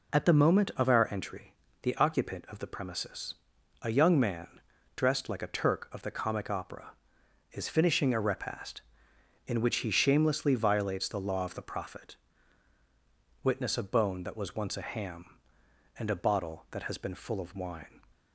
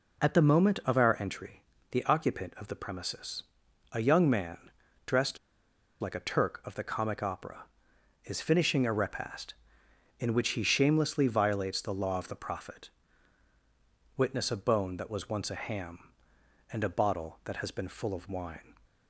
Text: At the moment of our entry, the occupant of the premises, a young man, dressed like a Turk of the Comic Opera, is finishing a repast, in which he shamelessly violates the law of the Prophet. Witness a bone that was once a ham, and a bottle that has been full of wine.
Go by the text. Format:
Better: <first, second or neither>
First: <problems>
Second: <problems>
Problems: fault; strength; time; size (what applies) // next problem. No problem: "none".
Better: first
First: none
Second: pauses between "dressed" and "like"; noticeable; at 5.3 s; 0.63 s long